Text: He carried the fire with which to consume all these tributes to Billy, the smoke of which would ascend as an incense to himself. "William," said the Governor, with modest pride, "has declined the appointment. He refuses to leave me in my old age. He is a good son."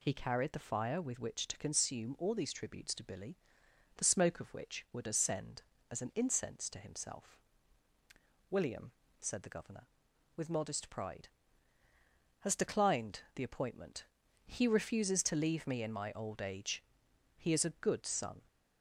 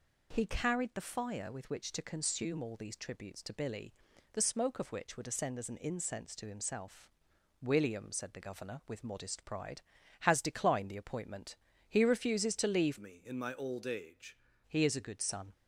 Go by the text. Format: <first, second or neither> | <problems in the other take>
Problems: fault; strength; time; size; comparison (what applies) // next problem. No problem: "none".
first | changes voice from "me" to "age"; from 12.9 to 14.3 s; 1.4 s long